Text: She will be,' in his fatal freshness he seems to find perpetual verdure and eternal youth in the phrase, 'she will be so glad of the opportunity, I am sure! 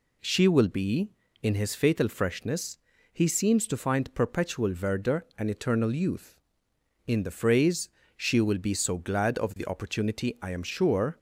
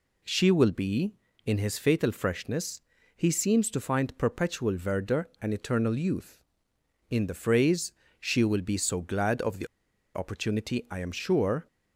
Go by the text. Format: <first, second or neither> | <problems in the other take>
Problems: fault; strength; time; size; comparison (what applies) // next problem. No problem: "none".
first | pauses between "freshness" and "he"; at 2.7 s; 0.38 s long; also in the first // pauses between "the" and "opportunity"; noticeable; at 9.6 s; 0.47 s long